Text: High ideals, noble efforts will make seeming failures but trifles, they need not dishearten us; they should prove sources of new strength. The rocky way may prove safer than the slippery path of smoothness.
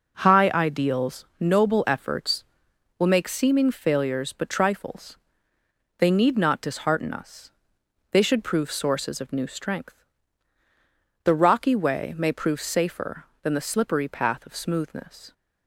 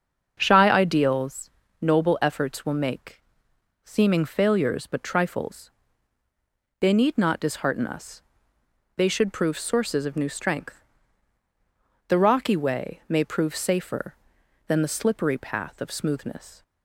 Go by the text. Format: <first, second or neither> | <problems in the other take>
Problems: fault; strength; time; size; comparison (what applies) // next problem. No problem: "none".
first | starts louder than the rest; until 1.4 s; 6.5 dB // says "Shy" for "High"; at 0.4 s // pauses between "make" and "seeming"; noticeable; at 3.2 s; 0.60 s long